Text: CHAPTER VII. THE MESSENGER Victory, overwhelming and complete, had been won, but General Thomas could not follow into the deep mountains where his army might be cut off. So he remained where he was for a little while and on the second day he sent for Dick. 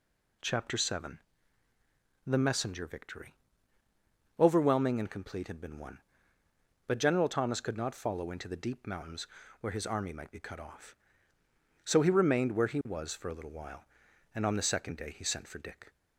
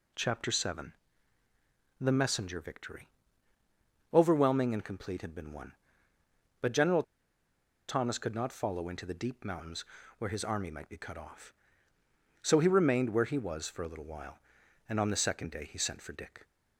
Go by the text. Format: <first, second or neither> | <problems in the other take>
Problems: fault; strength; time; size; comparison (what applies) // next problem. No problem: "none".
first | pauses between "General" and "Thomas"; noticeable; at 7.0 s; 0.85 s long // pauses between "mountains" and "where"; slight; at 9.8 s; 0.32 s long; slight in the first